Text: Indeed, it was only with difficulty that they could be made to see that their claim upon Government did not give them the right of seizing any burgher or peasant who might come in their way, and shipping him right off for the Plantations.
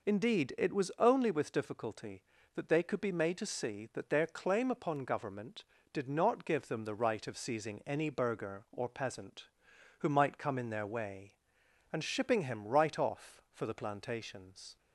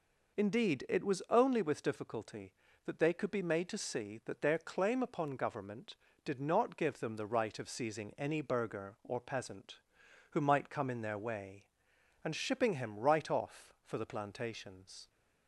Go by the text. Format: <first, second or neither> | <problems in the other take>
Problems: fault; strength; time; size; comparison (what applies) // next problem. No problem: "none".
neither | none